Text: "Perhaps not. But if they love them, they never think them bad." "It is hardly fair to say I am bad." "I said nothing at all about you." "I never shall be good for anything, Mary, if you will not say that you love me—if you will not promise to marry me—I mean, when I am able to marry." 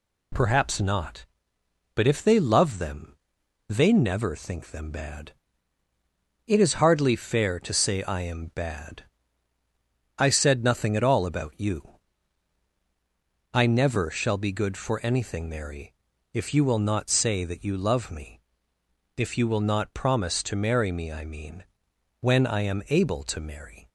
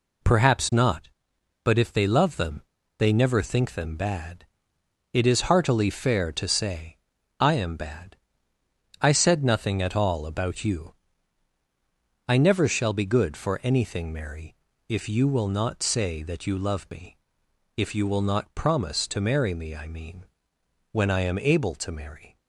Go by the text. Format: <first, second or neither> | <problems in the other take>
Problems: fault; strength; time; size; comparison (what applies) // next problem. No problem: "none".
first | says "heartily" for "hardly"; at 5.5 s // pauses between "say" and "I"; at 6.9 s; 0.42 s long